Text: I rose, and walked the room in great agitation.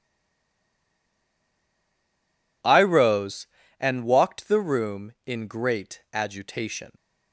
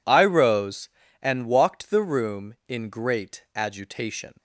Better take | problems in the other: second | stays silent before the first word; strong; until 2.6 s; 2.6 s long

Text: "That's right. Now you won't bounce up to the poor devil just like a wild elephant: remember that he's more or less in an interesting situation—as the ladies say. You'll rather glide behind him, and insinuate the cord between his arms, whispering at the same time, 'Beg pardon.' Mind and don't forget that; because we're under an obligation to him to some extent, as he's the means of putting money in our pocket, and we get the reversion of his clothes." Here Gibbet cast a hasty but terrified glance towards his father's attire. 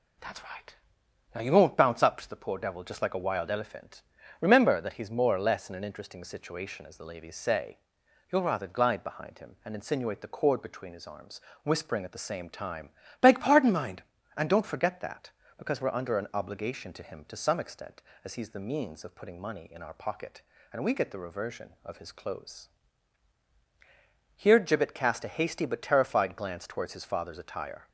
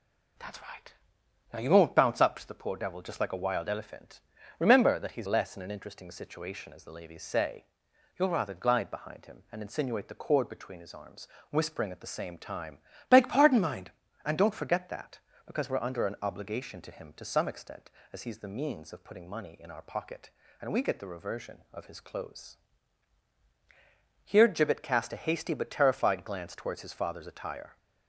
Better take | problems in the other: first | skips "more or"; at 5.2 s

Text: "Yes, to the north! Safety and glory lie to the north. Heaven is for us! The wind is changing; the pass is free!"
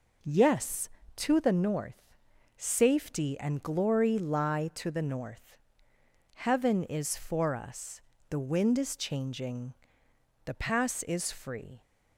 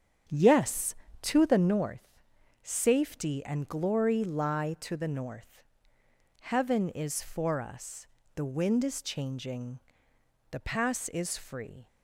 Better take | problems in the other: first | starts louder than the rest; strong; until 2.1 s; 8 dB

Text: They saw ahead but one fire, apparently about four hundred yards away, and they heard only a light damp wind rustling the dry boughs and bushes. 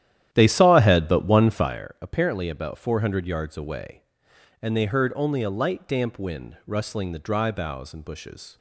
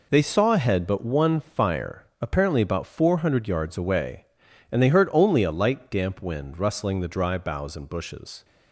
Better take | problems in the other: second | starts louder than the rest; strong; until 1.8 s; 11.5 dB

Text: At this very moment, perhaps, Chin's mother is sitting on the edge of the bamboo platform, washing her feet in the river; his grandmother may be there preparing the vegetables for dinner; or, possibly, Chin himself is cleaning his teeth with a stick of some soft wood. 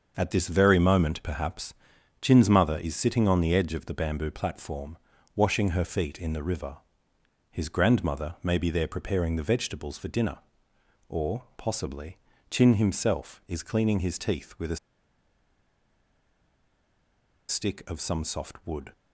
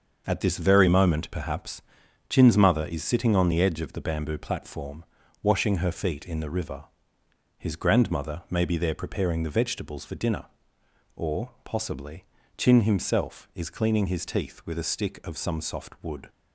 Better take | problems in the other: second | starts louder than the rest; until 1.1 s; 6.5 dB; also in the second // pauses between "a" and "stick"; strong; at 14.7 s; 2.7 s long

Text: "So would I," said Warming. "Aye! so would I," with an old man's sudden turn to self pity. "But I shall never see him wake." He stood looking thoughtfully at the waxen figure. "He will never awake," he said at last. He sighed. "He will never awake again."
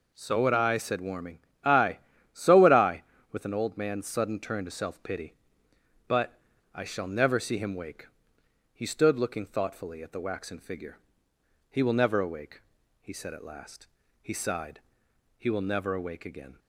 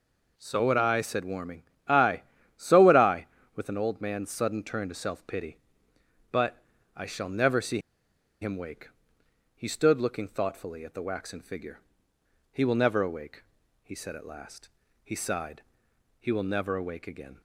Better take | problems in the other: first | pauses between "But" and "I"; slight; at 6.6 s; 0.32 s long; slight in the first // pauses between "see" and "him"; noticeable; at 7.7 s; 0.63 s long

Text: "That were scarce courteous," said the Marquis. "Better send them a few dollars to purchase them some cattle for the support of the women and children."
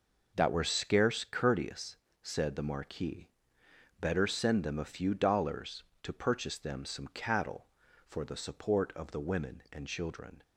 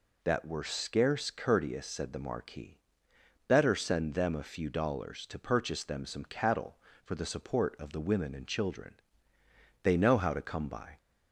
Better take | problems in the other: first | goes on to say "They know how to come by"; noticeable; from 9.8 s on; 1.1 s long

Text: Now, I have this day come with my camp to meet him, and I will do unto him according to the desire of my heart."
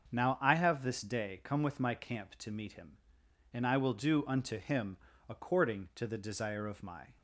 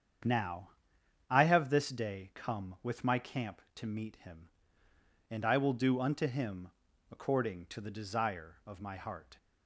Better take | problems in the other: second | starts louder than the rest; until 1.1 s; 7 dB; strong in the second // pauses between "him" and "according"; slight; at 4.9 s; 0.32 s long; also in the second // stops before "heart"; at 7.1 s

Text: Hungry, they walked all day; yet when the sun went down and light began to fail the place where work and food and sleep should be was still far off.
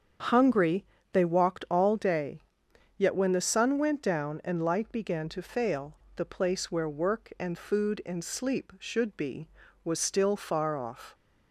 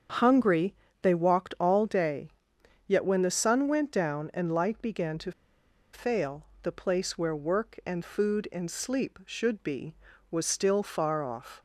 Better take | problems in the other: first | starts louder than the rest; strong; until 1.3 s; 7.5 dB; strong in the first // pauses between "to" and "fail"; noticeable; at 5.3 s; 0.62 s long // pauses between "fail" and "the"; slight; at 6.4 s; 0.16 s long; slight in the first

